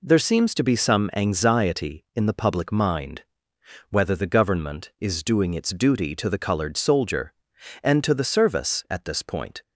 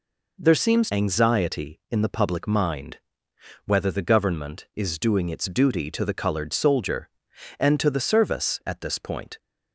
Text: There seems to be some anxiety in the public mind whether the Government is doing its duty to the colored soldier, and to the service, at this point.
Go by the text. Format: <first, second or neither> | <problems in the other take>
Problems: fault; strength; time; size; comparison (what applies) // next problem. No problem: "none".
first | skips "to be some"; at 0.8 s // pauses between "mind" and "whether"; noticeable; at 2.9 s; 0.66 s long; noticeable in the first